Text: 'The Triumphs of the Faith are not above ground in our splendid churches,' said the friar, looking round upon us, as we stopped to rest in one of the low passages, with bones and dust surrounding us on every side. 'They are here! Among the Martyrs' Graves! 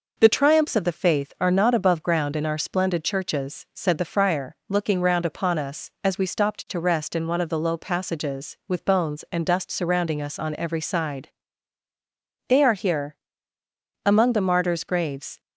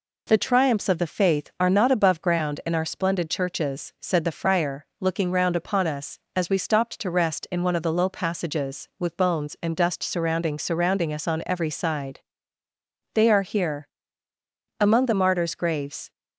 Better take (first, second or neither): first